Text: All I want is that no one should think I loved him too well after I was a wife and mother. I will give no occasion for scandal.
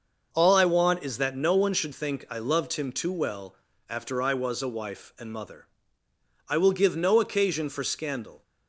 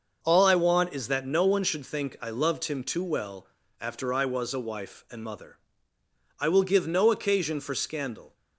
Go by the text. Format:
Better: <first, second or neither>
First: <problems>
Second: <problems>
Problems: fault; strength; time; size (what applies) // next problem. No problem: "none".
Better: neither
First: starts louder than the rest; noticeable; until 1.3 s; 6 dB // pauses between "well" and "after"; slight; at 3.5 s; 0.32 s long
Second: starts louder than the rest; noticeable; until 1.2 s; 6 dB // pauses between "well" and "after"; slight; at 3.4 s; 0.32 s long